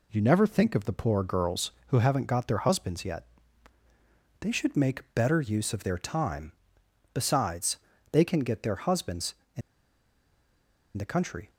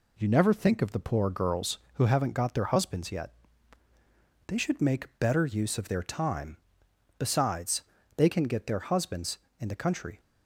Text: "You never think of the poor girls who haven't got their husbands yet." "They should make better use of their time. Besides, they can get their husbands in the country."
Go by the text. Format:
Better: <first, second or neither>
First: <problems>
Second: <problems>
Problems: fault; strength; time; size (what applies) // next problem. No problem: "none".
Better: second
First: pauses between "in" and "the"; strong; at 9.6 s; 1.3 s long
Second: none